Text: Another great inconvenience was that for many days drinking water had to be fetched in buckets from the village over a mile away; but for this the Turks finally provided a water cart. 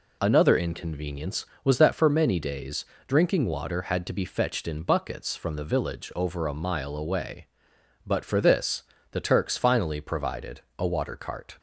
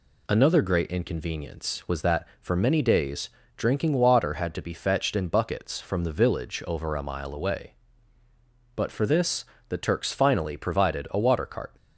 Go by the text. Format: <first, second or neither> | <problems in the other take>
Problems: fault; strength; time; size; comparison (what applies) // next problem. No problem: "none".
second | skips "great"; at 0.5 s // pauses between "days" and "drinking"; slight; at 2.8 s; 0.22 s long; slight in the second // pauses between "this" and "the"; slight; at 8.8 s; 0.30 s long; slight in the second // pauses between "provided" and "a"; slight; at 10.6 s; 0.16 s long